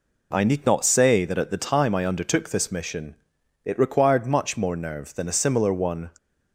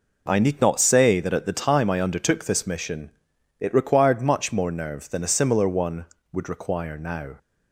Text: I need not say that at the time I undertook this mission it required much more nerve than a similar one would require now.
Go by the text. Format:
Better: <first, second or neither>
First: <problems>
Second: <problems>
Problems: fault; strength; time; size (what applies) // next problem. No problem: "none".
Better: second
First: pauses between "mission" and "it"; noticeable; at 3.1 s; 0.50 s long // stops before "would require now"; at 6.1 s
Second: pauses between "mission" and "it"; noticeable; at 3.1 s; 0.50 s long